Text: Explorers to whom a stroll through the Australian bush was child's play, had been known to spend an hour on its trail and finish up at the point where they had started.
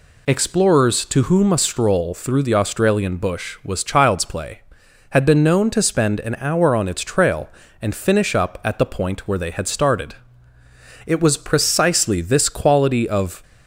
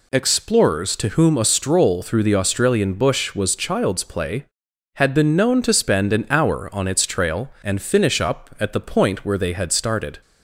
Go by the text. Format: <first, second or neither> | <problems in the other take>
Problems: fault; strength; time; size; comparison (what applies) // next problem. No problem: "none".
second | goes on to say "It was precisely this quality of"; strong; from 11.0 s on; 2.3 s long